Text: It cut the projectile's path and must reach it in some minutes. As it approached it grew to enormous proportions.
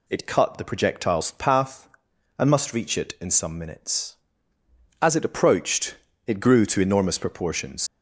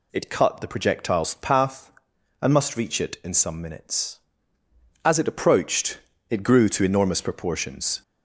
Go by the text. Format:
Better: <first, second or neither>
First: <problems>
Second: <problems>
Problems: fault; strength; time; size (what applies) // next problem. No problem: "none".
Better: second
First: pauses between "approached" and "it"; slight; at 5.9 s; 0.30 s long // leaves "proportions" unfinished; at 7.8 s; 120 ms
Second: pauses between "approached" and "it"; slight; at 5.9 s; 0.30 s long